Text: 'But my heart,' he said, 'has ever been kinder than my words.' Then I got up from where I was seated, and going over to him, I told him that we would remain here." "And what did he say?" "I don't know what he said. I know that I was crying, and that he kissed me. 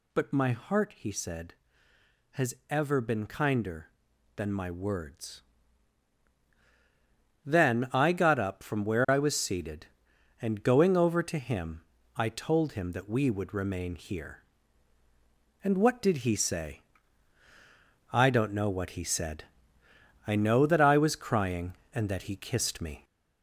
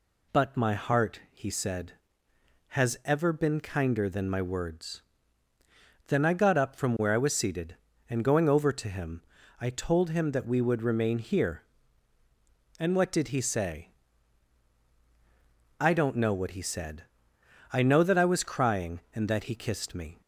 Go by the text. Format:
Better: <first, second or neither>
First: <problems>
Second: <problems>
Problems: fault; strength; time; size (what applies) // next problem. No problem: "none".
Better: second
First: gets louder; noticeable; throughout; 4 dB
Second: none